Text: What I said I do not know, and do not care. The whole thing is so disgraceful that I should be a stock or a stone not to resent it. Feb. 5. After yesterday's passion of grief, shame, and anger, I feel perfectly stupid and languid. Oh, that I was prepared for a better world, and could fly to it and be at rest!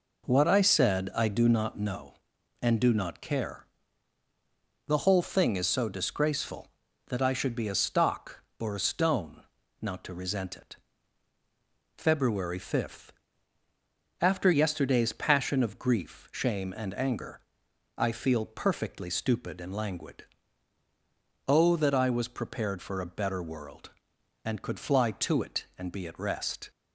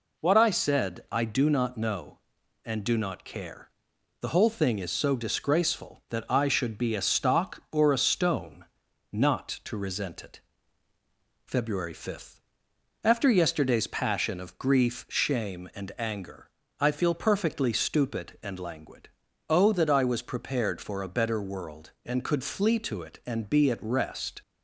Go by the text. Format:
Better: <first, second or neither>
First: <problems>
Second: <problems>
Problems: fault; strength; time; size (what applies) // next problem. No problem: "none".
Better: first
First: pauses between "stone" and "not"; at 9.4 s; 0.40 s long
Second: pauses between "stone" and "not"; noticeable; at 8.6 s; 0.48 s long // says "flee" for "fly"; at 22.4 s